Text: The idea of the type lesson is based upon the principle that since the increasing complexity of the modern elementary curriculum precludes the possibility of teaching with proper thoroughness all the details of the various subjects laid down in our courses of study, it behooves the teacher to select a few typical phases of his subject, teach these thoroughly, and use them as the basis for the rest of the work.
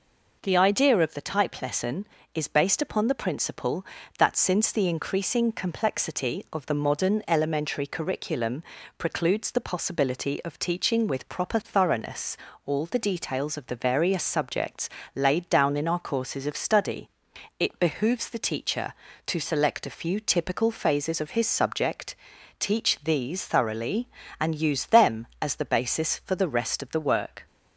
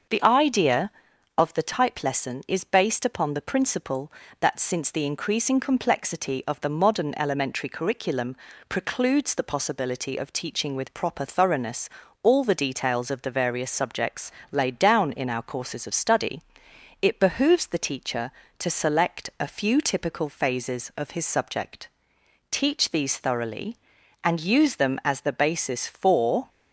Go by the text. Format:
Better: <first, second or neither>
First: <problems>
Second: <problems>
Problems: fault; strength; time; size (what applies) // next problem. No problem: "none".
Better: first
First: pauses between "curriculum" and "precludes"; slight; at 8.6 s; 0.34 s long // pauses between "thoroughness" and "all"; slight; at 12.3 s; 0.30 s long // pauses between "subjects" and "laid"; slight; at 14.8 s; 0.26 s long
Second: starts louder than the rest; until 1.5 s; 6.5 dB // pauses between "curriculum" and "precludes"; slight; at 8.3 s; 0.32 s long // pauses between "thoroughness" and "all"; slight; at 11.8 s; 0.34 s long // pauses between "subjects" and "laid"; slight; at 14.3 s; 0.22 s long // stops before "the rest of the work"; at 26.4 s